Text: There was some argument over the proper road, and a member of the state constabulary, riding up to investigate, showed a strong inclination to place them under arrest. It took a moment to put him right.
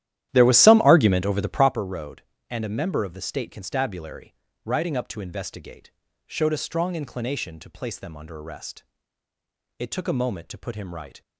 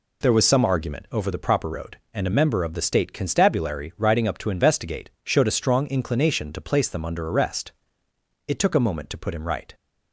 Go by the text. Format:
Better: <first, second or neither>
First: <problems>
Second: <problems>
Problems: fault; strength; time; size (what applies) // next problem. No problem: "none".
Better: second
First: starts louder than the rest; strong; until 1.8 s; 12.5 dB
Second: none